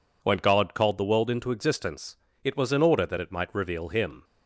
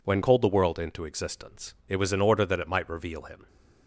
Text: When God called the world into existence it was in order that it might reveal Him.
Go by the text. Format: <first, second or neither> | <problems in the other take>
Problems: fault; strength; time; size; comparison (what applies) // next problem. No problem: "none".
first | skips "God"; at 0.2 s // pauses between "existence" and "it"; slight; at 1.7 s; 0.16 s long; slight in the first